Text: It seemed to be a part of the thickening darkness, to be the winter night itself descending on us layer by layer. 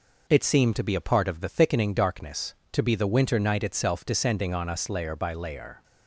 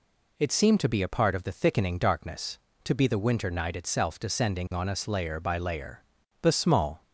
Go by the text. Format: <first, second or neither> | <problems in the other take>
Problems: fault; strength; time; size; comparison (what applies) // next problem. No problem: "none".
first | goes on to say "The small"; noticeable; from 6.3 s on; 0.62 s long